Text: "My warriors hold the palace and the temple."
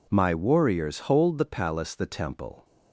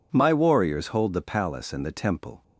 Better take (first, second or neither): second